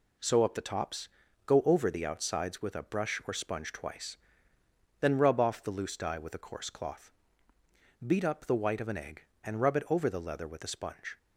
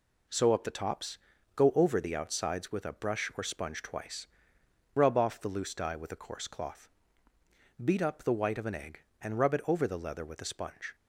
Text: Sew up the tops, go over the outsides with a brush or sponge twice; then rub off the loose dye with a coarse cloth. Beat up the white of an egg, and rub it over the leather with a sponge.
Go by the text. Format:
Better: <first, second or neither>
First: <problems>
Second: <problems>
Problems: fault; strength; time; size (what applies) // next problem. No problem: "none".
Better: first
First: none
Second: skips "then"; at 4.6 s